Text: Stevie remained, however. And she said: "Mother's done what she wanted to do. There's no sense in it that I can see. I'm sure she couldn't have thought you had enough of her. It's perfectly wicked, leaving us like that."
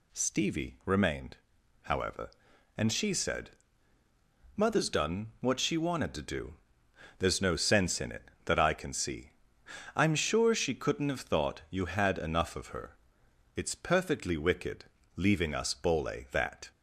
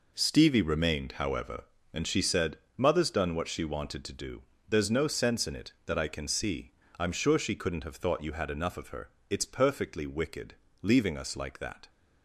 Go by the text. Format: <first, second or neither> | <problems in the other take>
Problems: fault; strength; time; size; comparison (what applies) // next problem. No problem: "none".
second | says "bole" for "like"; at 15.7 s